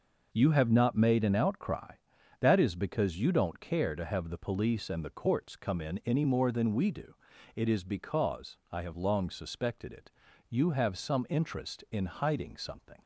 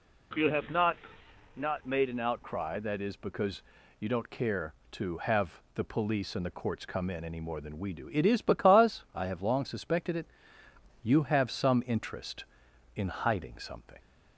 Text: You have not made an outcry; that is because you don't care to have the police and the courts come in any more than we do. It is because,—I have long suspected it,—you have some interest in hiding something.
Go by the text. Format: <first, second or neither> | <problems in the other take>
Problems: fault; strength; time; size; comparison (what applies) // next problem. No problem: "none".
first | says "not" twice; at 1.5 s // pauses between "because" and "you"; at 3.5 s; 0.40 s long